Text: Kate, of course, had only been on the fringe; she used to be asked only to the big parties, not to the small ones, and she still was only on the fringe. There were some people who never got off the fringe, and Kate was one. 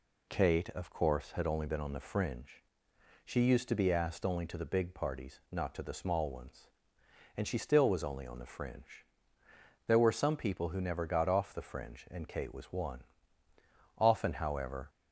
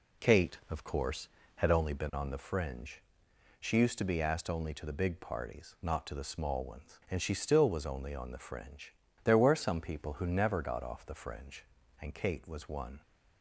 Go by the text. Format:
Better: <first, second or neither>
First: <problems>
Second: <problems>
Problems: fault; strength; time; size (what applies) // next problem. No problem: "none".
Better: second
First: goes on to say "Often however"; noticeable; from 13.9 s on; 0.92 s long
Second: none